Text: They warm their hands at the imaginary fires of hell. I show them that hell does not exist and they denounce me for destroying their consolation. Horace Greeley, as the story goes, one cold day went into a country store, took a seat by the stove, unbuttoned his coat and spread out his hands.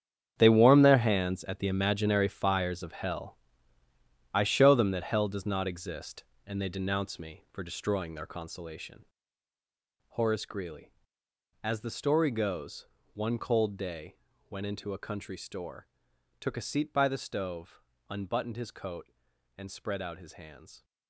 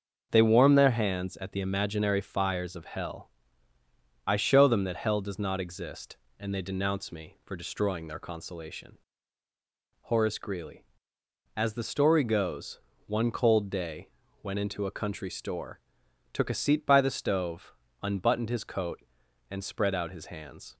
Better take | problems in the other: second | gets quieter; strong; throughout; 13 dB // starts louder than the rest; strong; until 1.3 s; 8.5 dB; also in the second // pauses between "day" and "went"; slight; at 14.1 s; 0.34 s long; slight in the second

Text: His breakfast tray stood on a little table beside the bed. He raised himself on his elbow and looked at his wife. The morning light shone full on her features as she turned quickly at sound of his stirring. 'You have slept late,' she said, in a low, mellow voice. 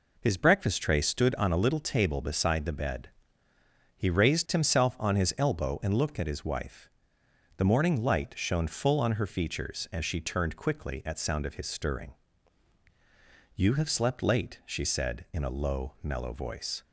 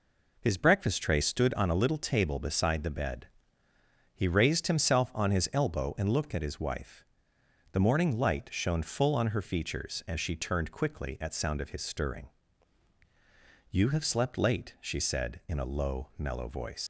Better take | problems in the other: first | leaves "voice" unfinished; at 16.8 s; 110 ms

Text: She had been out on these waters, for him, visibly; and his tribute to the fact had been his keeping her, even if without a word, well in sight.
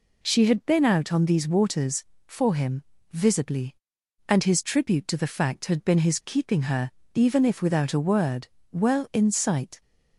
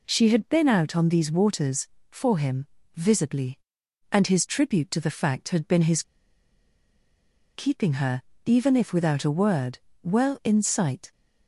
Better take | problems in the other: first | pauses between "his" and "keeping"; strong; at 6.0 s; 1.5 s long

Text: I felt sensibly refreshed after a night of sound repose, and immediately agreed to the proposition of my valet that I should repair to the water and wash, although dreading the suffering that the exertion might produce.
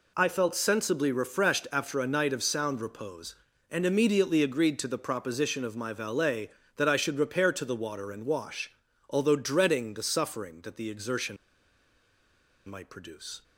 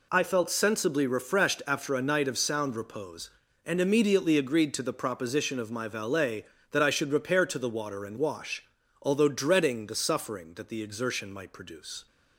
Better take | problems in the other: second | pauses between "exertion" and "might"; strong; at 11.3 s; 1.3 s long

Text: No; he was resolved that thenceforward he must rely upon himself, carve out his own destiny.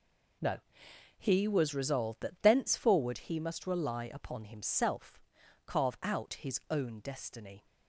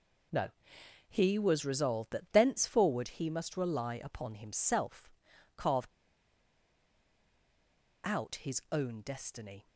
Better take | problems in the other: first | pauses between "carve" and "out"; strong; at 5.8 s; 2.1 s long

